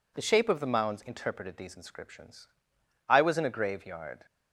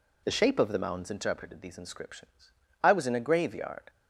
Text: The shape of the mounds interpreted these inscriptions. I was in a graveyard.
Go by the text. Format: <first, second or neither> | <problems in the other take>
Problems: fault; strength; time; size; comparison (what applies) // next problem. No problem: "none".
neither | none